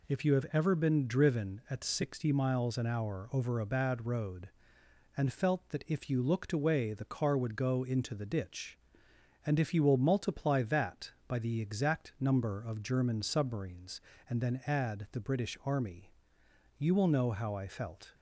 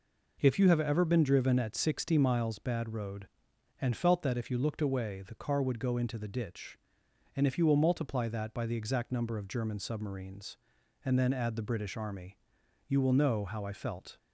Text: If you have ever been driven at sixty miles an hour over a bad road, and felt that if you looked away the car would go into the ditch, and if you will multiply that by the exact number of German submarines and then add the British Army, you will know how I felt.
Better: first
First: none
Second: skips "an hour over a"; at 2.5 s

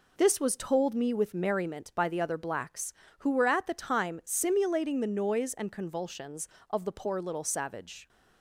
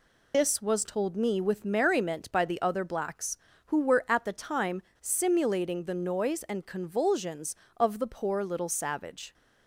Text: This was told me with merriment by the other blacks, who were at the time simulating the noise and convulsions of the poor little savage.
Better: first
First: none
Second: loses the start of "This"; at 0.3 s; 150 ms // pauses between "time" and "simulating"; slight; at 4.8 s; 0.19 s long

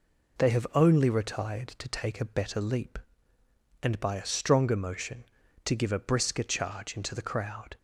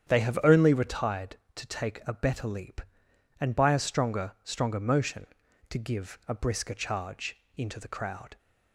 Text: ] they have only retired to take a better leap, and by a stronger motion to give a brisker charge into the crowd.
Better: first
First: none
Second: starts louder than the rest; strong; until 1.1 s; 8.5 dB // says "stronger" twice; at 4.4 s // pauses between "charge" and "into"; slight; at 7.3 s; 0.20 s long

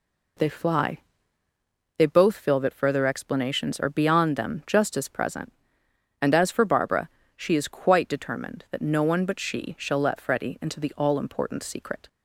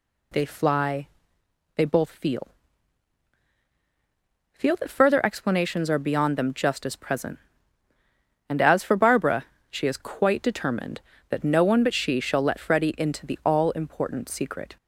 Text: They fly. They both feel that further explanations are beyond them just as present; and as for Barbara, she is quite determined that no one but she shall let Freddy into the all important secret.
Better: first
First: none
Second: says "feel" twice; at 4.5 s

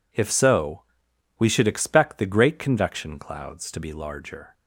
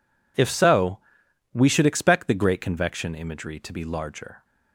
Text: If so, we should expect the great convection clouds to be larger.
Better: first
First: none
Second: says "imagery" for "clouds"; at 3.1 s

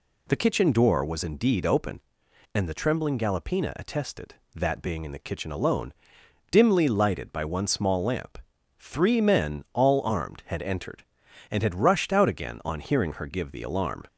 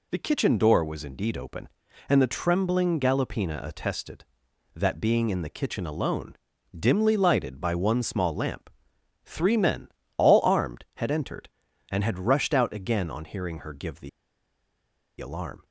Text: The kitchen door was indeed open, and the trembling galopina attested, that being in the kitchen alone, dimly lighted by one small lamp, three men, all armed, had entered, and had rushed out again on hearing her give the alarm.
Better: first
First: none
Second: pauses between "the" and "alarm"; at 14.0 s; 1.1 s long

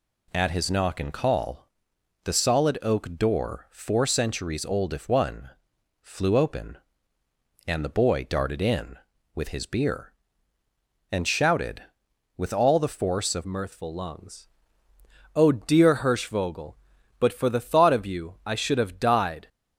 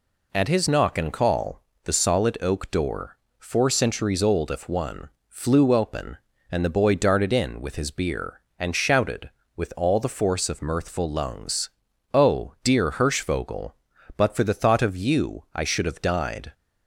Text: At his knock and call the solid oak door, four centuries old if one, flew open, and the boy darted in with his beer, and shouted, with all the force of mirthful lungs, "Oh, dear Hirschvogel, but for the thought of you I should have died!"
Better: second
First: pauses between "call" and "the"; noticeable; at 1.6 s; 0.56 s long // changes voice at "mirthful"; from 13.4 s on; 6.0 s long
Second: pauses between "call" and "the"; slight; at 1.6 s; 0.24 s long

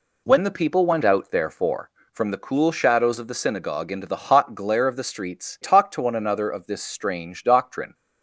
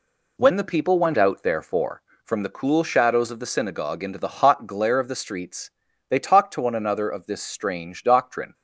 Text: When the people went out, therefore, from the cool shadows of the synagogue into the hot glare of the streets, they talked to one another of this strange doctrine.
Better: second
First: skips "they"; at 5.5 s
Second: none

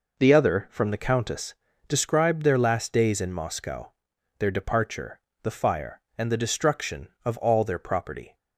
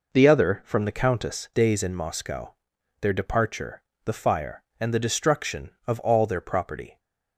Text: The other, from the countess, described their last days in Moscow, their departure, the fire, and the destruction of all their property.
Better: first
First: none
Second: skips "described their last"; at 1.5 s

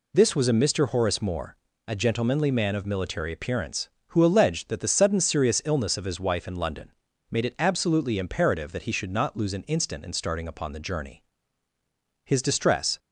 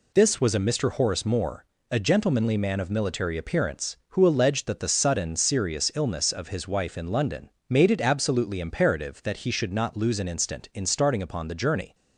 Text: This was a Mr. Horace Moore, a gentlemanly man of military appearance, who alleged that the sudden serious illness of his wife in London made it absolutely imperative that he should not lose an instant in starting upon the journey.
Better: second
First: pauses between "London" and "made"; at 6.9 s; 0.38 s long // goes on to say "His distress"; noticeable; from 12.2 s on; 0.74 s long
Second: pauses between "London" and "made"; slight; at 7.5 s; 0.18 s long

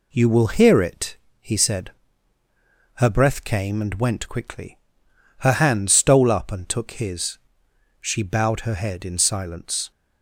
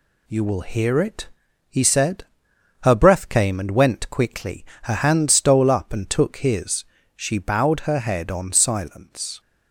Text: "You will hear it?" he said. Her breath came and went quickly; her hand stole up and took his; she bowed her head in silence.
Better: first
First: none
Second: says "on" for "in"; at 8.3 s

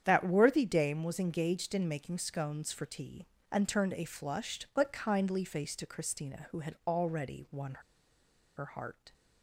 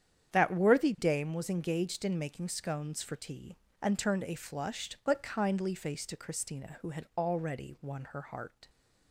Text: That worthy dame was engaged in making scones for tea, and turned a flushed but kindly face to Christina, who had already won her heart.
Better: second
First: starts louder than the rest; strong; until 1.0 s; 8.5 dB // pauses between "won" and "her"; noticeable; at 7.7 s; 0.82 s long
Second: starts louder than the rest; strong; until 1.3 s; 8.5 dB

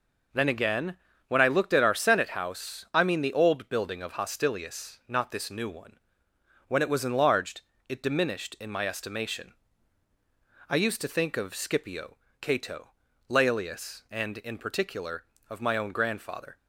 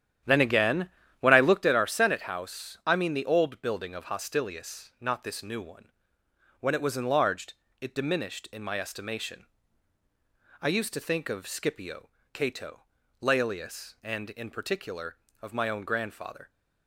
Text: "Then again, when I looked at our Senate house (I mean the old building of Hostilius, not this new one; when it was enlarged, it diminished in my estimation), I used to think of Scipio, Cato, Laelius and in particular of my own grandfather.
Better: first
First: none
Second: starts louder than the rest; strong; until 1.7 s; 10.5 dB

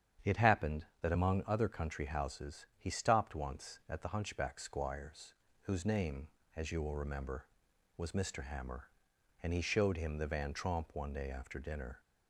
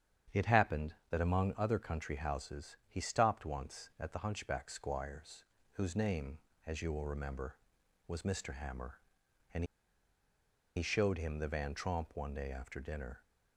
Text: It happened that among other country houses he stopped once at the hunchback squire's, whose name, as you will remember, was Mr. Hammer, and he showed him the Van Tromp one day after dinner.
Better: first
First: starts louder than the rest; strong; until 1.3 s; 8.5 dB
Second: starts louder than the rest; strong; until 1.4 s; 8.5 dB // pauses between "and" and "he"; at 9.6 s; 1.1 s long

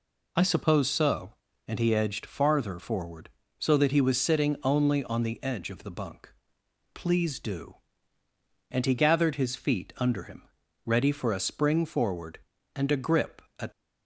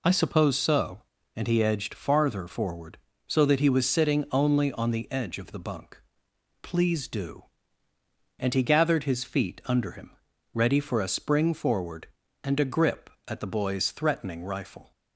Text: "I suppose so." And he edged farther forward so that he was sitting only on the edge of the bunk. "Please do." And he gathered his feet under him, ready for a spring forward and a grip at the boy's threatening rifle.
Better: second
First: stops before "the boy's threatening rifle"; at 13.7 s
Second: none

